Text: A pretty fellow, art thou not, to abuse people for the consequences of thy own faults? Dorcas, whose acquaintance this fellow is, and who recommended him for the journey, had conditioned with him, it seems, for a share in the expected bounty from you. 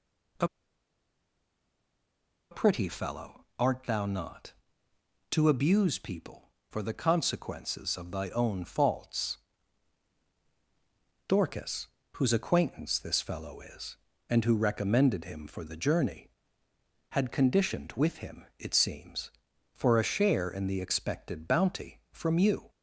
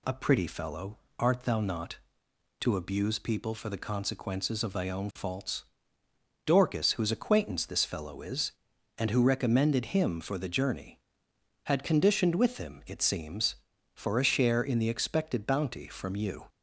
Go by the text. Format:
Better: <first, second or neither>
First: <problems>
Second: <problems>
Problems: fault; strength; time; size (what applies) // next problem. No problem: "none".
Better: second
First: pauses between "A" and "pretty"; strong; at 0.4 s; 2.0 s long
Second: none